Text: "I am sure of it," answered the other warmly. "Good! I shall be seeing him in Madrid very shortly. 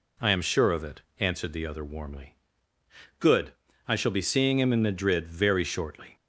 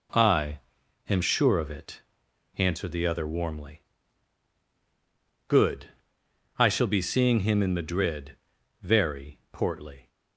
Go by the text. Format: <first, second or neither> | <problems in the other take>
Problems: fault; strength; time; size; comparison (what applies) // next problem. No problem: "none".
first | pauses between "I" and "am"; noticeable; at 0.5 s; 0.50 s long // pauses between "Madrid" and "very"; noticeable; at 8.3 s; 0.48 s long // says "portly" for "shortly"; at 9.5 s